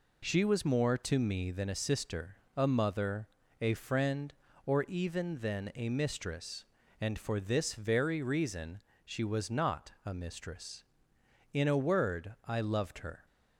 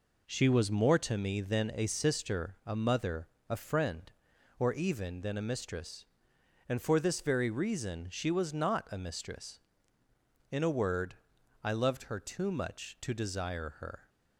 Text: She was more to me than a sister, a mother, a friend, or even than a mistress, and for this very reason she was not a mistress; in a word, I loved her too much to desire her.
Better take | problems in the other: second | pauses between "reason" and "she"; slight; at 8.7 s; 0.24 s long // stops before "too much to desire her"; at 13.2 s

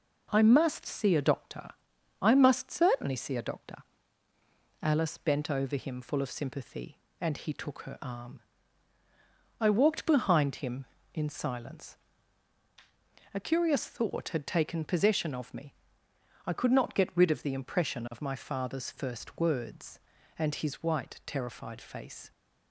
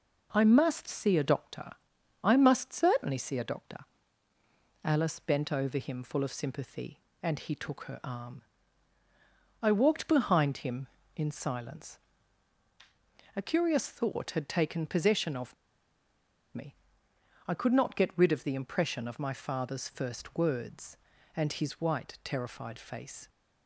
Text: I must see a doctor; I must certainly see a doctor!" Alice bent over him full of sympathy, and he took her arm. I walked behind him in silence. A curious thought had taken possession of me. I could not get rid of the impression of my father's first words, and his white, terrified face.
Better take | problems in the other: first | pauses between "of" and "me"; at 15.5 s; 1.0 s long

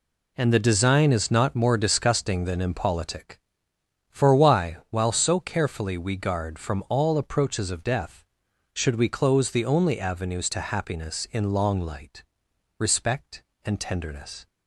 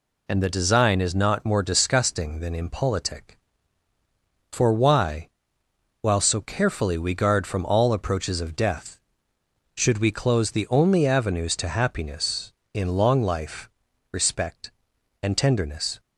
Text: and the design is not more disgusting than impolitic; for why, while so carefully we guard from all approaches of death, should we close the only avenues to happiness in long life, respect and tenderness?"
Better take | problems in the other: second | says "light" for "life"; at 11.8 s

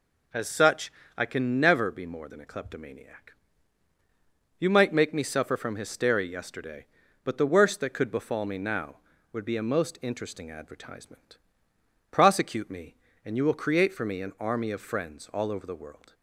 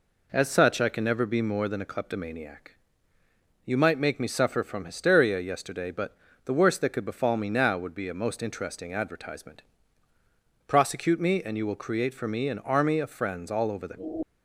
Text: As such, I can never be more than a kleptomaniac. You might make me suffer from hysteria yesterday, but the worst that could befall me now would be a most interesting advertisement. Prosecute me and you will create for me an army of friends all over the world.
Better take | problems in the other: first | pauses between "but" and "the"; slight; at 6.1 s; 0.30 s long // stops before "world"; at 14.2 s

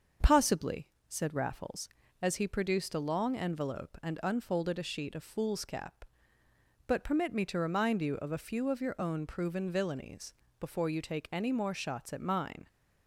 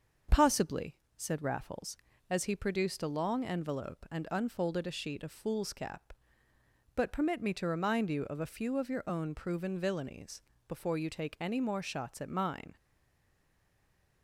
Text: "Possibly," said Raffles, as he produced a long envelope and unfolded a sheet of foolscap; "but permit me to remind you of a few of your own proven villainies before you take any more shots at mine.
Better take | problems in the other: first | starts louder than the rest; until 1.5 s; 6.5 dB; also in the first // pauses between "villainies" and "before"; slight; at 10.4 s; 0.26 s long; slight in the first // stays silent after the last word; noticeable; from 12.7 s on; 1.5 s long

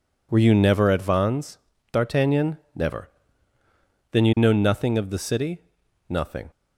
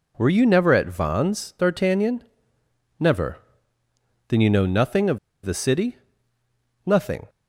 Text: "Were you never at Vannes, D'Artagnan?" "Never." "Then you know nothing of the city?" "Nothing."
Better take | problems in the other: first | pauses between "of" and "the"; slight; at 5.1 s; 0.25 s long

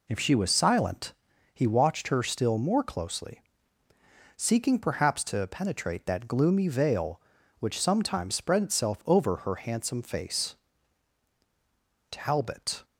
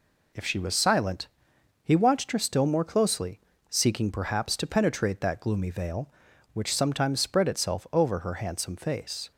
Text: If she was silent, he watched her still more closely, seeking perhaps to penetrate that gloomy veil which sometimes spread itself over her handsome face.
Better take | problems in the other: second | goes on to say "Talbot"; noticeable; from 12.1 s on; 0.74 s long

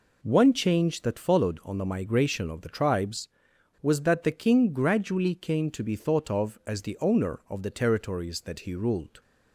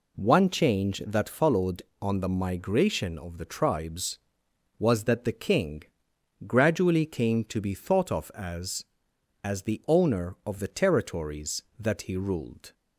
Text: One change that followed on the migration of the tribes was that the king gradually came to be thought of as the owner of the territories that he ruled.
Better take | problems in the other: first | pauses between "king" and "gradually"; noticeable; at 5.8 s; 0.60 s long // says "as" twice; at 9.4 s

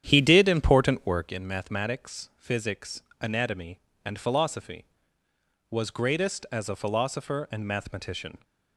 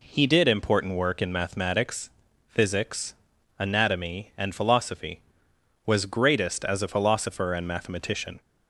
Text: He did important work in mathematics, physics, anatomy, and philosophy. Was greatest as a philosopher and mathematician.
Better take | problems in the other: second | starts louder than the rest; strong; until 1.4 s; 9.5 dB

